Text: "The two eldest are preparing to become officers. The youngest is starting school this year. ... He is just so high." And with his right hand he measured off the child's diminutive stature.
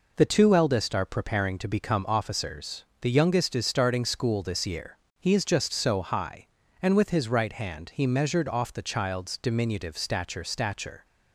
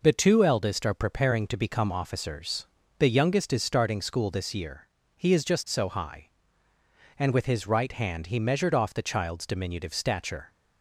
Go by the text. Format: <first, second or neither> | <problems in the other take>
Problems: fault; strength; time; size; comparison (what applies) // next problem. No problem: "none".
second | says "stature" twice; at 10.4 s